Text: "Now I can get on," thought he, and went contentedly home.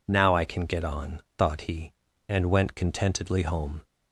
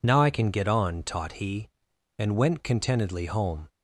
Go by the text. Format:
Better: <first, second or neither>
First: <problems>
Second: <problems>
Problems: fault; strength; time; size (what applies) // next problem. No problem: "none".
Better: first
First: none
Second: says "taught" for "thought"; at 1.0 s